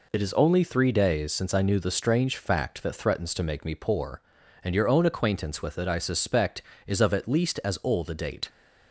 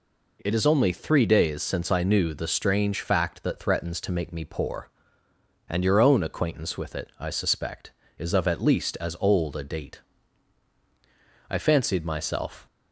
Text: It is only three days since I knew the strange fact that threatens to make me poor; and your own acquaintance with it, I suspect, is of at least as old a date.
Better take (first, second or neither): first